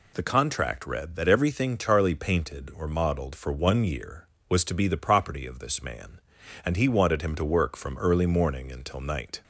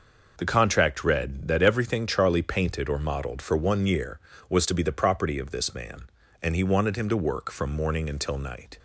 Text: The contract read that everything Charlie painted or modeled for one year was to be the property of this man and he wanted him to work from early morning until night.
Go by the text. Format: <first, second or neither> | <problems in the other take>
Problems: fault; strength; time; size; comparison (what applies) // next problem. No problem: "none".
first | skips "early"; at 7.7 s